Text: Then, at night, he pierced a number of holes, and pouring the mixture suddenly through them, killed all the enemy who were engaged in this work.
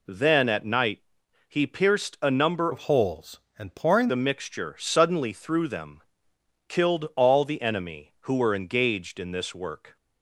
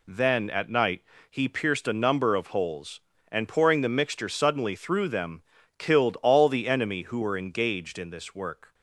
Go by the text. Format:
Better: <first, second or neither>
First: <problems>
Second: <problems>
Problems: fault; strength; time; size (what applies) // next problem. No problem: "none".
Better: second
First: changes voice from "of" to "pouring"; from 2.7 to 4.0 s; 1.3 s long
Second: none